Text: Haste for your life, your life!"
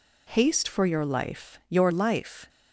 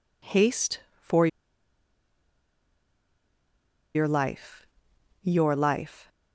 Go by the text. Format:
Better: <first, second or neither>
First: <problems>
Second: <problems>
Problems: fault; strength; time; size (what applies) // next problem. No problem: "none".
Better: first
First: none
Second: pauses between "for" and "your"; strong; at 1.2 s; 2.6 s long